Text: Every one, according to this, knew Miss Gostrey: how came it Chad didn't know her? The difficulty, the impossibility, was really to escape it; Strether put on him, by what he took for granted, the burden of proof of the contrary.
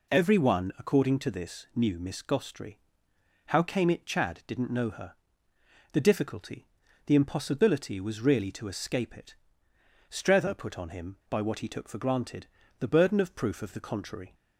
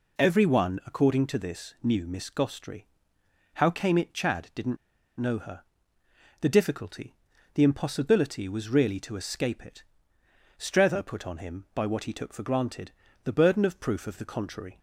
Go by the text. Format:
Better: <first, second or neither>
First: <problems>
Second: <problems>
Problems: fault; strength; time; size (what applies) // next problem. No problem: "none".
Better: first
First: none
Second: pauses between "didn't" and "know"; at 4.7 s; 0.43 s long